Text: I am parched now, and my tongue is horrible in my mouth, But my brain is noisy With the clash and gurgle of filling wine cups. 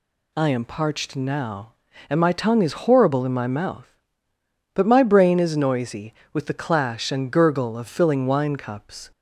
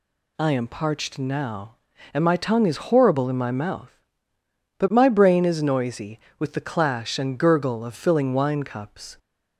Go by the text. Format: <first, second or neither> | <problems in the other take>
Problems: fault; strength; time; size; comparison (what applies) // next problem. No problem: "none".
neither | none